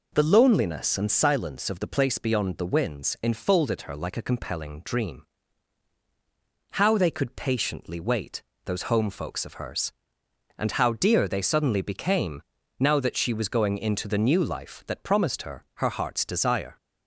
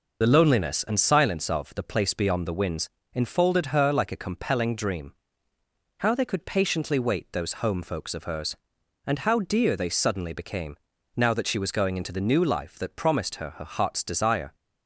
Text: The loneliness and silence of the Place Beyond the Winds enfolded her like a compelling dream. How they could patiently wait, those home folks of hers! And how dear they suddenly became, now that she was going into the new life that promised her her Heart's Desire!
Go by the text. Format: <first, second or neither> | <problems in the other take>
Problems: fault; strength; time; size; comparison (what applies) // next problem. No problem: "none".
first | loses the start of "The"; at 0.2 s; 45 ms // pauses between "Winds" and "enfolded"; slight; at 2.8 s; 0.24 s long